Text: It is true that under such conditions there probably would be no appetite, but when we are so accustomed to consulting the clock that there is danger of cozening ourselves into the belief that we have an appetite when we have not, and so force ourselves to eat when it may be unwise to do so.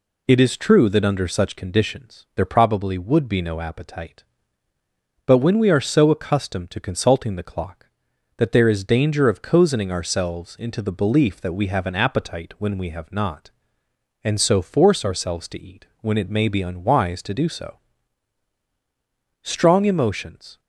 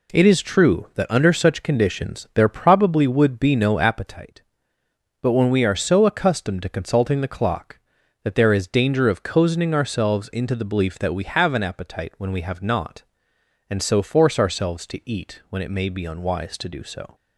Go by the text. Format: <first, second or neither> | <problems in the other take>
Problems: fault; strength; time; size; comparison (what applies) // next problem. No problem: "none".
second | goes on to say "Strong emotions"; noticeable; from 19.4 s on; 1.1 s long